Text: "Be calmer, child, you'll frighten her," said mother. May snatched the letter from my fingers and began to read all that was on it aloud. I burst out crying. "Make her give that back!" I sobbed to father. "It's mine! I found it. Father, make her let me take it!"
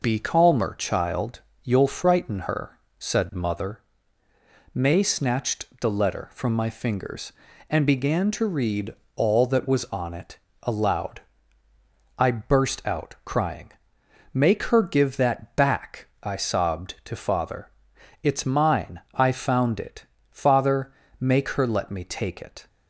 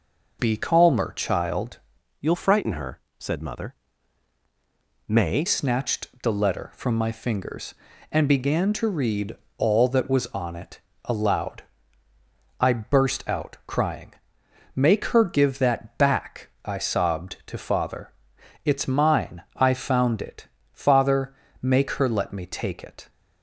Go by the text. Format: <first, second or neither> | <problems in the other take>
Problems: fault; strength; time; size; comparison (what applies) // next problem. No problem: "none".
first | changes voice from "you'll" to "May"; from 2.1 to 5.4 s; 3.3 s long // pauses between "snatched" and "the"; slight; at 6.0 s; 0.16 s long; slight in the first // pauses between "read" and "all"; slight; at 9.3 s; 0.22 s long; slight in the first // pauses between "it" and "aloud"; slight; at 10.7 s; 0.24 s long; slight in the first